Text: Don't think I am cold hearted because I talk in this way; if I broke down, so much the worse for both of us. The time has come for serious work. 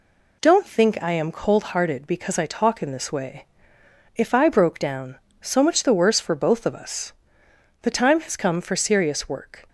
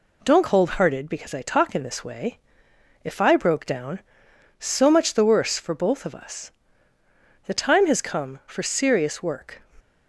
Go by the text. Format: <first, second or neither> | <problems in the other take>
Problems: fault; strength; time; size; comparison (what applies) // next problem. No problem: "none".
first | skips "think I am"; at 0.4 s